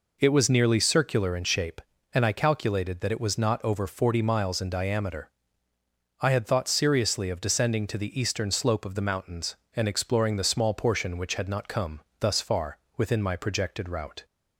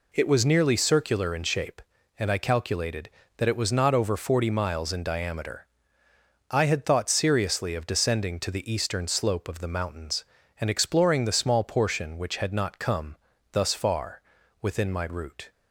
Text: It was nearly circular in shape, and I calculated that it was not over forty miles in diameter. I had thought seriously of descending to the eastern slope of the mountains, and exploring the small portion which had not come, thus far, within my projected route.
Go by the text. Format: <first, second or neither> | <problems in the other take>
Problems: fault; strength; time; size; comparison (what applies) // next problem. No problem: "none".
first | skips "projected"; at 15.0 s